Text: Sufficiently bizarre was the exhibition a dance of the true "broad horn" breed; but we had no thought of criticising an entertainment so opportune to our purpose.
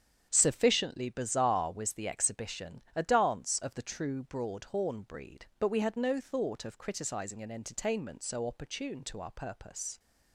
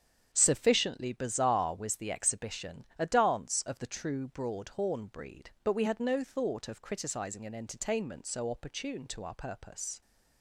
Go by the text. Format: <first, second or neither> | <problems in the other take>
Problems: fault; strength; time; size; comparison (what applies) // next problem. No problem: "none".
neither | starts louder than the rest; strong; the same in both // pauses between "exhibition" and "a"; slight; the same in both